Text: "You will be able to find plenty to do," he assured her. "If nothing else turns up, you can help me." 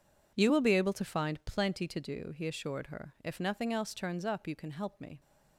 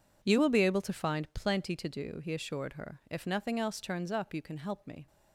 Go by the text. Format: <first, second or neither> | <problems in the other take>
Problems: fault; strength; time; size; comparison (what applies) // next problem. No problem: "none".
neither | none